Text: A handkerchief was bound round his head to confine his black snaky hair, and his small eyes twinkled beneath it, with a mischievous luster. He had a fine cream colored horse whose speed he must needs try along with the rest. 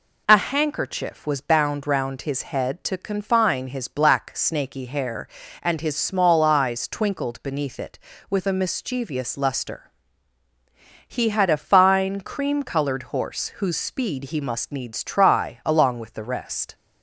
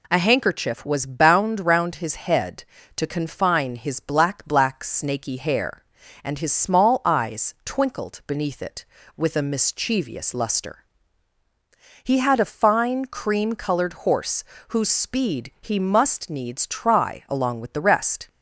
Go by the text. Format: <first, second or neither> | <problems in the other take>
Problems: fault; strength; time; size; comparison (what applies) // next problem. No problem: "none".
first | says "black" twice; at 4.4 s // pauses between "horse" and "whose"; slight; at 14.4 s; 0.24 s long